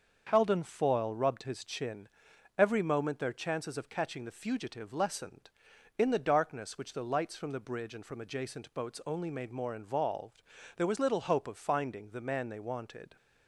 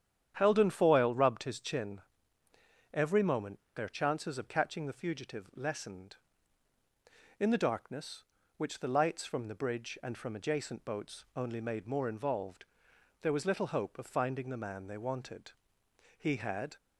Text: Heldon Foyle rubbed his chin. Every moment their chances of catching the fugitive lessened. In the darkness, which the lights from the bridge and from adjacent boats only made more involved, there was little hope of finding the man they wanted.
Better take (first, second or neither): first